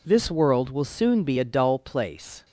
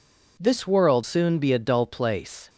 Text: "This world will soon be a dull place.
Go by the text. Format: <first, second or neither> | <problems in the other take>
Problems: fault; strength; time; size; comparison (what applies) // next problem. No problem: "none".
first | skips "will"; at 1.0 s